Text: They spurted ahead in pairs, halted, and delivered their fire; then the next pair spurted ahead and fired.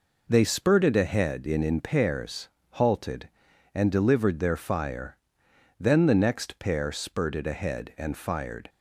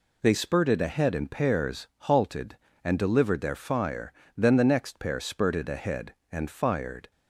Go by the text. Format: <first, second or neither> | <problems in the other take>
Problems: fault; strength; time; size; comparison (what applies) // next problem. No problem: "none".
second | says "in" twice; at 1.6 s